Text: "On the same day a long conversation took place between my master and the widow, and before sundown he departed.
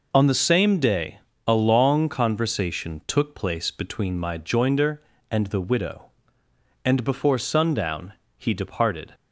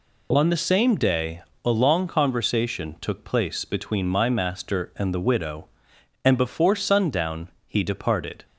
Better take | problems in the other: second | pauses between "day" and "a"; slight; at 1.1 s; 0.28 s long; slight in the second // says "joinder" for "master"; at 4.3 s // pauses between "sundown" and "he"; slight; at 8.1 s; 0.24 s long; slight in the second

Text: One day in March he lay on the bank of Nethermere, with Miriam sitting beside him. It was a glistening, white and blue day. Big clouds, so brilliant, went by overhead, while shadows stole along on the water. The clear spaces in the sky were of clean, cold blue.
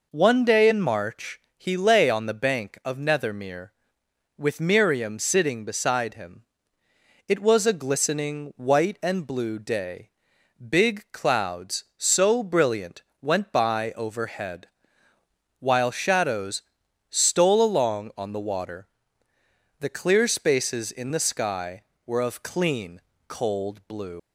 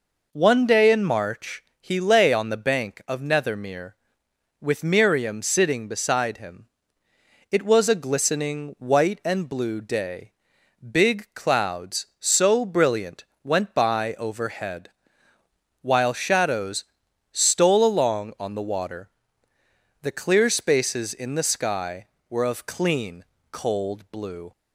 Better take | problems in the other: second | pauses between "March" and "he"; slight; at 1.3 s; 0.18 s long; slight in the second // pauses between "shadows" and "stole"; noticeable; at 16.6 s; 0.48 s long; noticeable in the second // leaves "blue" unfinished; at 24.1 s; 80 ms

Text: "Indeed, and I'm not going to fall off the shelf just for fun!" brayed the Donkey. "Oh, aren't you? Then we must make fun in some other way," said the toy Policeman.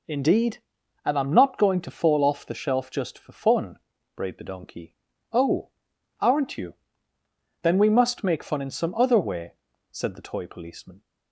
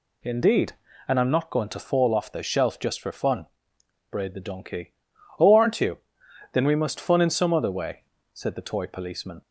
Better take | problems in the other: first | skips "make"; at 6.9 s

